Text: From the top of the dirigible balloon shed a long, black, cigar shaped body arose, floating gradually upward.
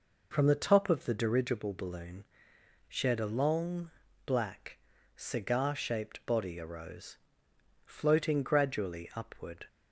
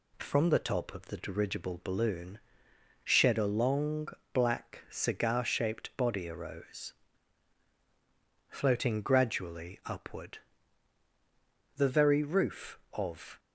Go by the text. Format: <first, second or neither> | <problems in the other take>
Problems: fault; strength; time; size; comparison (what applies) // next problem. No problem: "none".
first | pauses between "balloon" and "shed"; noticeable; at 2.3 s; 0.64 s long; noticeable in the first // goes on to say "The very roof of"; from 11.7 s on; 1.6 s long